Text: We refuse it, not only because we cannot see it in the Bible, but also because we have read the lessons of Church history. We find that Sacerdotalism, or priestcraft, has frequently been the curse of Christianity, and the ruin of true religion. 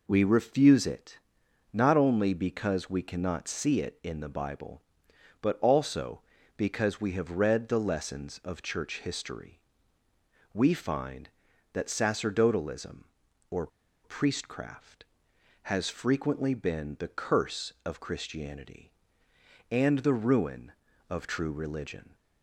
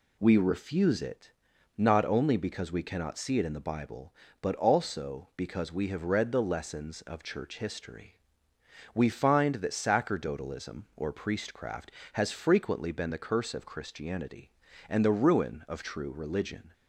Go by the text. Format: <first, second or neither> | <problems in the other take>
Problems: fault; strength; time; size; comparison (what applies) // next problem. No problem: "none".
second | pauses between "or" and "priestcraft"; at 13.6 s; 0.36 s long